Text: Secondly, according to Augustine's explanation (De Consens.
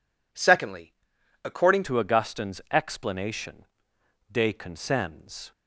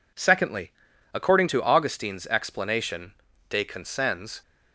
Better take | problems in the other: second | changes voice at "to"; from 1.8 s on; 3.7 s long

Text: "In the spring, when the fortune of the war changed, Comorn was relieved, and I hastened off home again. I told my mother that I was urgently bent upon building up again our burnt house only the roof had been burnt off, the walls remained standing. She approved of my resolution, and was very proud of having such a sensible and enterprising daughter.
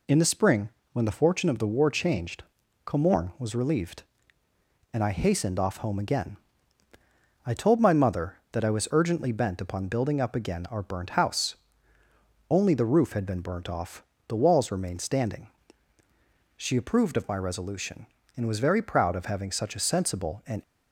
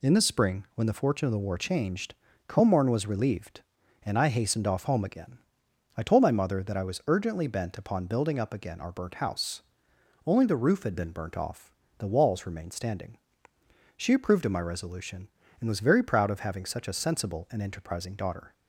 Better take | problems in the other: second | pauses between "house" and "only"; noticeable; at 11.5 s; 0.94 s long; noticeable in the second // stops before "enterprising daughter"; at 20.6 s

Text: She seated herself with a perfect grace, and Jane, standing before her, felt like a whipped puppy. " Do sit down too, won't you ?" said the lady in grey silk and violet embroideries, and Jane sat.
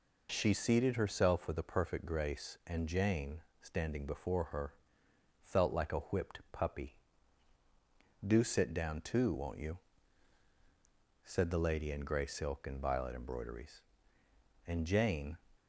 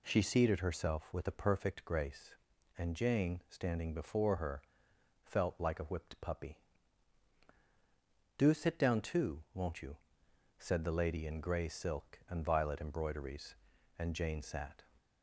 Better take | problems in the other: second | stops before "sat"; at 15.5 s

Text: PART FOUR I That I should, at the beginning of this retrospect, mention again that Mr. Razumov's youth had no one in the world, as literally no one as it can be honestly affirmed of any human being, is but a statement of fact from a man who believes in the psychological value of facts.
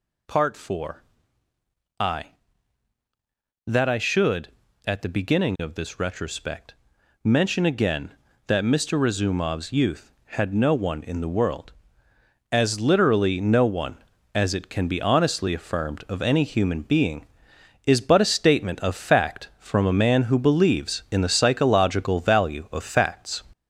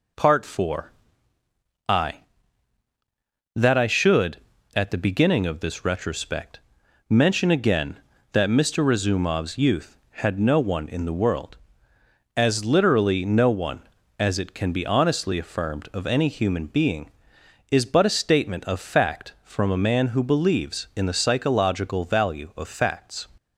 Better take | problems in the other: second | gets louder; noticeable; throughout; 4.5 dB // pauses between "FOUR" and "I"; noticeable; at 1.0 s; 0.96 s long; noticeable in the second

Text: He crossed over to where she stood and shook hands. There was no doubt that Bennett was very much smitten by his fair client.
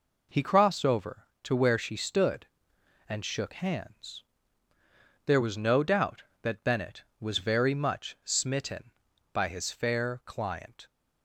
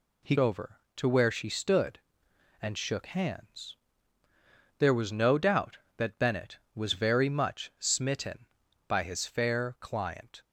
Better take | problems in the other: first | skips "crossed"; at 0.3 s

